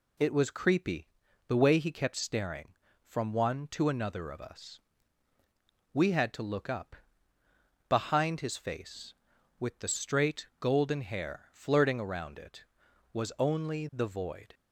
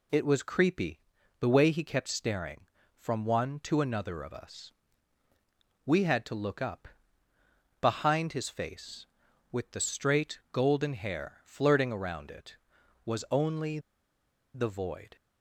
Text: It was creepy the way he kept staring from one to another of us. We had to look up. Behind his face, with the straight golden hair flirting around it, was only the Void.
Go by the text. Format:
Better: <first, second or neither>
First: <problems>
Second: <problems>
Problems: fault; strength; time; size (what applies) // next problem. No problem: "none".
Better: first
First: pauses between "creepy" and "the"; at 1.0 s; 0.40 s long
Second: pauses between "creepy" and "the"; at 0.9 s; 0.40 s long // pauses between "only" and "the"; noticeable; at 13.7 s; 0.75 s long